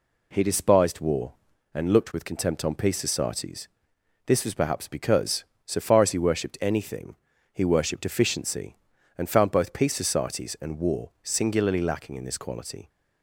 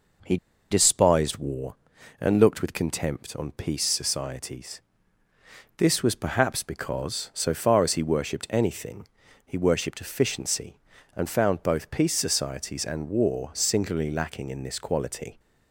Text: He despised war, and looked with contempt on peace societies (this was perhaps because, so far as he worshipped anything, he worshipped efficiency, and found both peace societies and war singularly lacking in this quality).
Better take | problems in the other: first | pauses between "He" and "despised"; slight; at 0.3 s; 0.34 s long

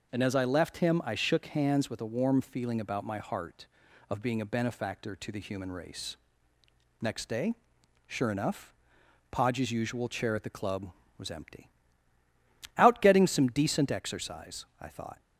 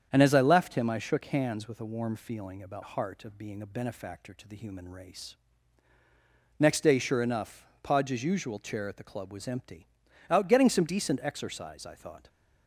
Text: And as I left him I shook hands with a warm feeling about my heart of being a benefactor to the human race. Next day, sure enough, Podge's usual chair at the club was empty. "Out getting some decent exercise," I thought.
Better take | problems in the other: first | starts louder than the rest; strong; until 1.1 s; 8 dB // skips "my"; at 2.8 s

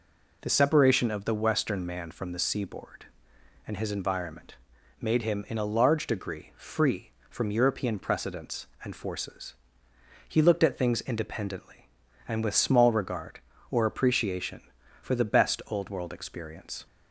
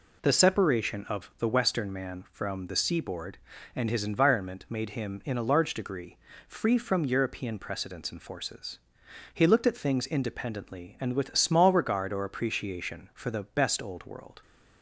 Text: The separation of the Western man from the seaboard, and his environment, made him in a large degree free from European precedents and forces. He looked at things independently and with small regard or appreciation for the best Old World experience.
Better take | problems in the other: first | pauses between "degree" and "free"; slight; at 6.1 s; 0.28 s long // stops before "experience"; at 14.4 s

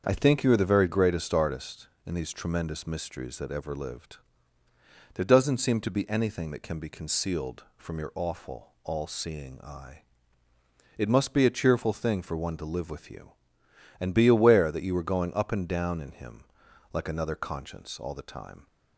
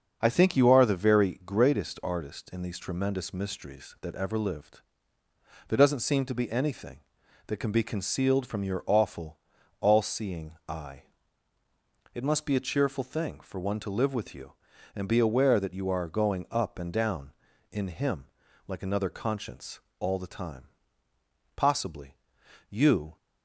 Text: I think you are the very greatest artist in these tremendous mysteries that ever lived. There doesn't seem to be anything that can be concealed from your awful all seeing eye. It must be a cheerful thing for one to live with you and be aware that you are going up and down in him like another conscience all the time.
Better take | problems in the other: first | starts louder than the rest; until 1.2 s; 6.5 dB; also in the first // pauses between "awful" and "all"; at 9.3 s; 0.42 s long // pauses between "him" and "like"; at 18.2 s; 0.42 s long; noticeable in the first // pauses between "conscience" and "all"; slight; at 19.8 s; 0.20 s long // goes on to say "Possibly you"; from 21.5 s on; 1.6 s long

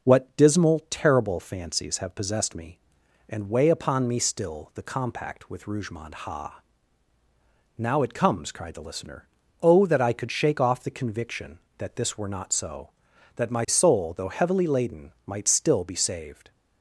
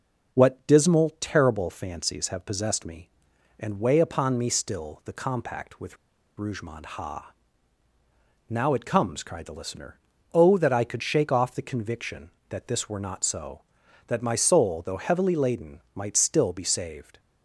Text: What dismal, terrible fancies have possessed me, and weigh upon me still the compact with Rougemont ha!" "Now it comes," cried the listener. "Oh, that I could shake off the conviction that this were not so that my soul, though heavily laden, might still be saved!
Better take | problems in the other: first | pauses between "with" and "Rougemont"; at 5.9 s; 0.43 s long

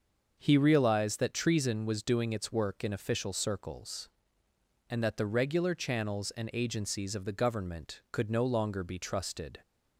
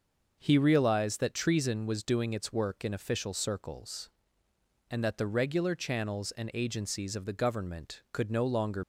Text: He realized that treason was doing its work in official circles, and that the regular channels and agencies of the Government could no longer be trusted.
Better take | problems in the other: first | starts louder than the rest; noticeable; until 1.4 s; 6 dB; also in the first // stops before "be trusted"; at 8.8 s

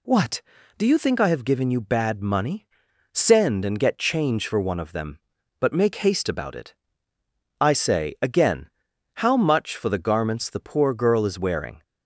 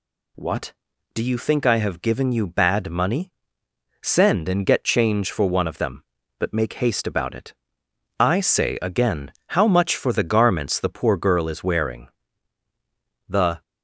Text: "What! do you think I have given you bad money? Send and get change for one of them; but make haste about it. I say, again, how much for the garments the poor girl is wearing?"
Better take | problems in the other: first | goes on to say "The"; slight; from 13.2 s on; 0.32 s long

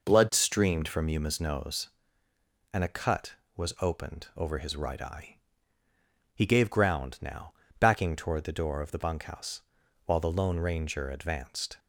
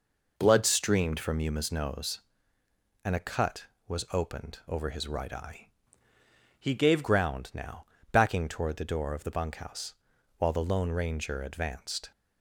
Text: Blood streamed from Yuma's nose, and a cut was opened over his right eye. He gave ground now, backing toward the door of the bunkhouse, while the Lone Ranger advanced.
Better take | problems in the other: first | changes voice from "He" to "gave"; from 6.5 to 7.0 s; 0.5 s long

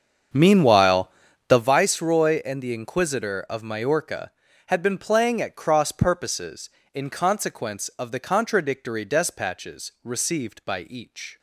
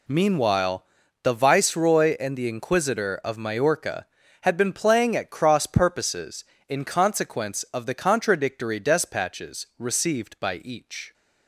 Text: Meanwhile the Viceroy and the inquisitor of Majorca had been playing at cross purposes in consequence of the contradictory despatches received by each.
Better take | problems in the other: second | starts louder than the rest; until 1.7 s; 7 dB // pauses between "Meanwhile" and "the"; at 1.1 s; 0.38 s long; also in the second

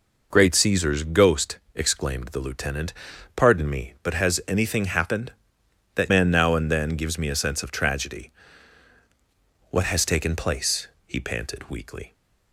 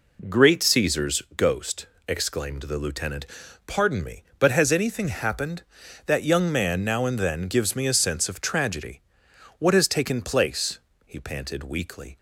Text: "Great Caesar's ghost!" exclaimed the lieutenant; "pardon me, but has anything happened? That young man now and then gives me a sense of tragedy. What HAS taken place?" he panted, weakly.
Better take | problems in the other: second | skips "young"; at 6.1 s

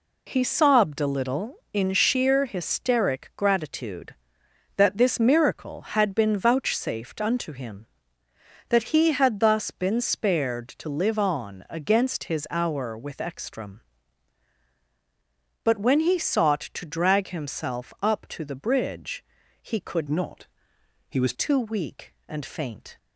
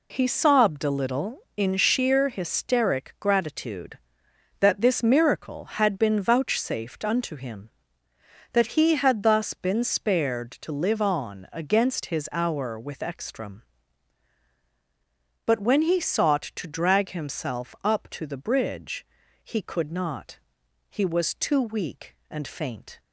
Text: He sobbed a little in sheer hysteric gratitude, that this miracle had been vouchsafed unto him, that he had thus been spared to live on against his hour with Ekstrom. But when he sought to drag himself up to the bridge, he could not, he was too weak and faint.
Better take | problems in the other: second | changes voice from "not" to "was"; from 20.0 to 21.3 s; 1.3 s long

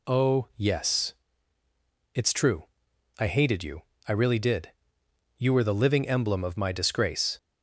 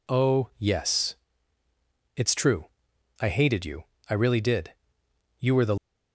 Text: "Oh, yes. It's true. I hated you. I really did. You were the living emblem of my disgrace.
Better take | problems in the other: first | stops before "living emblem of my disgrace"; at 5.7 s

